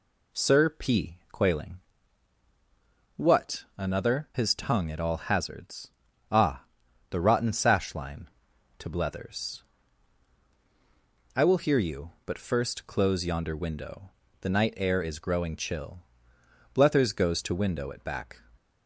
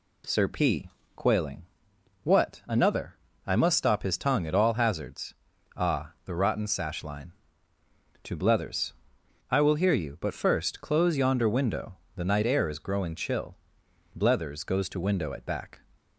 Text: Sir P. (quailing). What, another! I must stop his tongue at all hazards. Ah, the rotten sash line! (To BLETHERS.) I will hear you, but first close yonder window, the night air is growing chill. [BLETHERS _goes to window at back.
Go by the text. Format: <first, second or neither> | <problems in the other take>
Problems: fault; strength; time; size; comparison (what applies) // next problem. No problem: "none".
second | skips "I must stop"; at 4.3 s